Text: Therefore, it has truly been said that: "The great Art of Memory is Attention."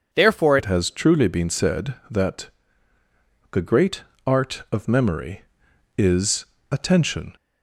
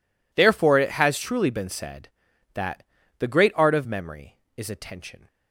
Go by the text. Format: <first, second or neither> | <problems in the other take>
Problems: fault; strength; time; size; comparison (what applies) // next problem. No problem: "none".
second | changes voice at "it"; from 0.5 s on; 6.8 s long // pauses between "great" and "Art"; slight; at 4.0 s; 0.24 s long // pauses between "is" and "Attention"; slight; at 6.4 s; 0.26 s long